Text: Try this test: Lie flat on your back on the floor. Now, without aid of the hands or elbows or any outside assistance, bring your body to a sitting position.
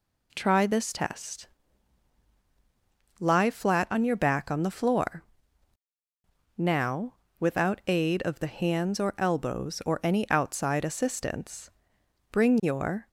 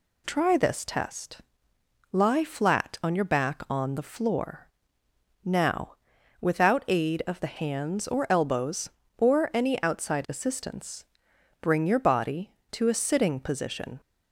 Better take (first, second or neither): second